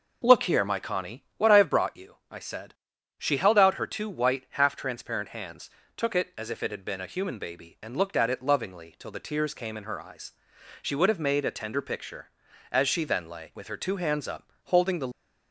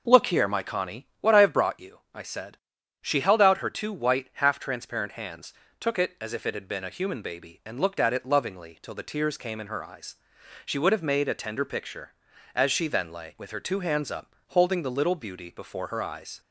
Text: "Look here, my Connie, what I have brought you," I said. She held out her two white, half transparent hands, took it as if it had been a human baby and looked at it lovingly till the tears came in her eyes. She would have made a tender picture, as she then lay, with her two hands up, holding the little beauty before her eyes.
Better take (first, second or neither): second